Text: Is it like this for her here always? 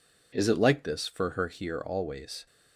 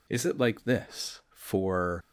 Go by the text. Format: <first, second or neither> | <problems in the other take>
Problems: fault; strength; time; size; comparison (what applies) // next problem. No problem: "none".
first | stops before "her here always"; at 2.0 s